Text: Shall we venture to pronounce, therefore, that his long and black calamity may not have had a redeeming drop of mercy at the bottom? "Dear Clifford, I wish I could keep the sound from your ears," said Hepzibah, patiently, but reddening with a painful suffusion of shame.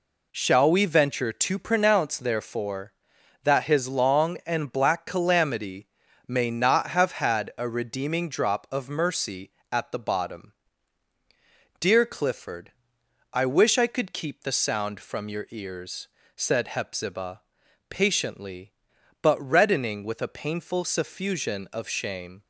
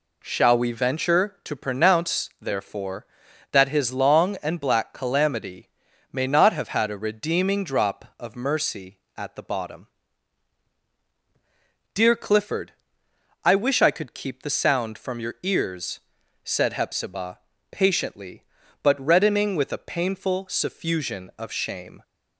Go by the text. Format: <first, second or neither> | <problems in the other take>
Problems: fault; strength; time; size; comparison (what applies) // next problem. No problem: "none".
neither | pauses between "calamity" and "may"; the same in both